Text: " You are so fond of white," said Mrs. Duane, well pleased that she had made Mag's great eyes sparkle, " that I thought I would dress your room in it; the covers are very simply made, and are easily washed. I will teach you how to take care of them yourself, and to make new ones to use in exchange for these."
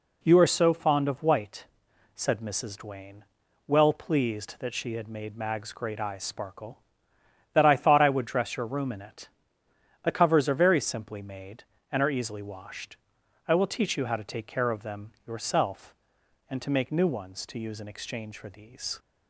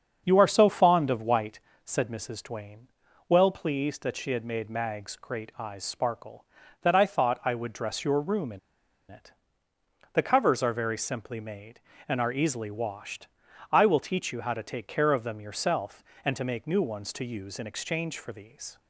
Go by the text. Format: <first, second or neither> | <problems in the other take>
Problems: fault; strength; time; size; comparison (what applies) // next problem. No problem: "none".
first | starts louder than the rest; strong; until 1.2 s; 7.5 dB // pauses between "in" and "it"; noticeable; at 8.5 s; 0.52 s long